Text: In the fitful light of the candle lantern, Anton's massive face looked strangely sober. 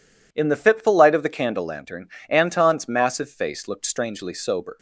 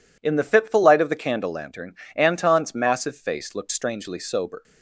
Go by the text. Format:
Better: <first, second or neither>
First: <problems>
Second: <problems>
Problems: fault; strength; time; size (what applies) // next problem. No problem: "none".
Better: neither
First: none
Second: none